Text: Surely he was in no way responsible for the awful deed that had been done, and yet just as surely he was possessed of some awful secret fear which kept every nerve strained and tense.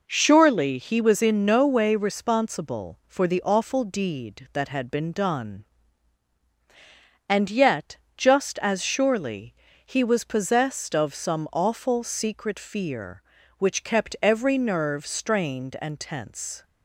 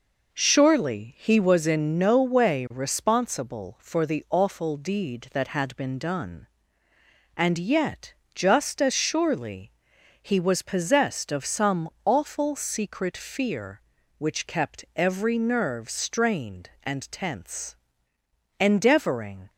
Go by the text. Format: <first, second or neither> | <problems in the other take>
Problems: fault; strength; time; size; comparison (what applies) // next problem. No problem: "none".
first | pauses between "yet" and "just"; slight; at 8.1 s; 0.20 s long; slight in the first // pauses between "surely" and "he"; noticeable; at 9.6 s; 0.50 s long; slight in the first // pauses between "some" and "awful"; slight; at 11.8 s; 0.16 s long // goes on to say "Endeavoring"; noticeable; from 18.5 s on; 0.92 s long